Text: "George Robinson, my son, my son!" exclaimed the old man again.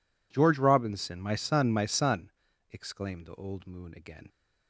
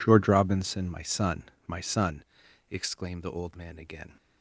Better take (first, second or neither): second